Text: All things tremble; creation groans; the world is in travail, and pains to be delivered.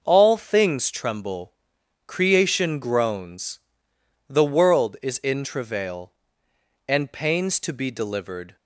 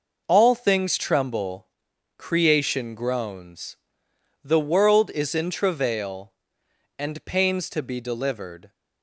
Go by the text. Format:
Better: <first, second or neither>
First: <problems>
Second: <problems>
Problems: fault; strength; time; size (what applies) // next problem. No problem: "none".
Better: neither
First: none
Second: none